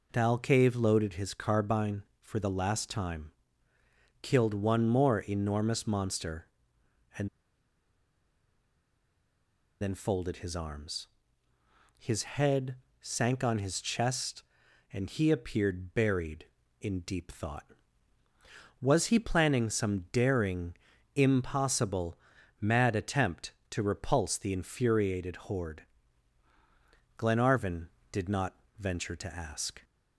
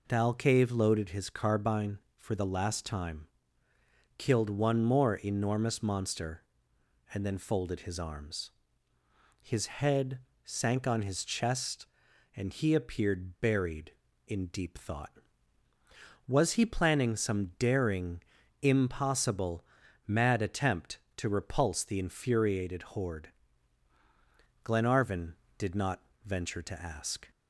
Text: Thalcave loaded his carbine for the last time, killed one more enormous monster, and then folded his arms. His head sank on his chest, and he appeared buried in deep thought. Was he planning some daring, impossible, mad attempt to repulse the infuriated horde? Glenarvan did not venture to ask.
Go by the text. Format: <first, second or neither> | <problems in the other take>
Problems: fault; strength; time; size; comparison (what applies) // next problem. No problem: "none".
second | pauses between "and" and "then"; strong; at 7.2 s; 2.5 s long // pauses between "head" and "sank"; slight; at 12.7 s; 0.26 s long; slight in the second // pauses between "not" and "venture"; slight; at 28.5 s; 0.24 s long; slight in the second